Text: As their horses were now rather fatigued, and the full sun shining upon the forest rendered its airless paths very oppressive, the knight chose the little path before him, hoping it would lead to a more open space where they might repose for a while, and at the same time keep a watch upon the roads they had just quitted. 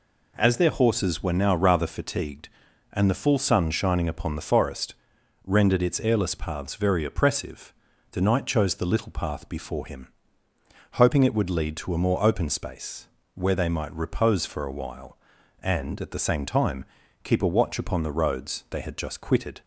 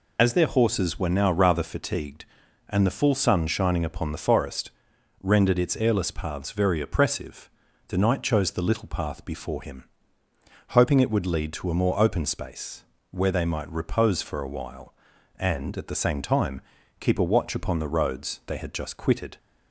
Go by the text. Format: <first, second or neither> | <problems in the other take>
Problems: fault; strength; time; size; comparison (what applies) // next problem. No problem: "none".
first | loses the start of "As"; at 0.1 s; 75 ms // pauses between "forest" and "rendered"; noticeable; at 4.7 s; 0.50 s long; noticeable in the first // pauses between "space" and "where"; slight; at 12.8 s; 0.28 s long; slight in the first // pauses between "time" and "keep"; at 16.6 s; 0.38 s long; also in the first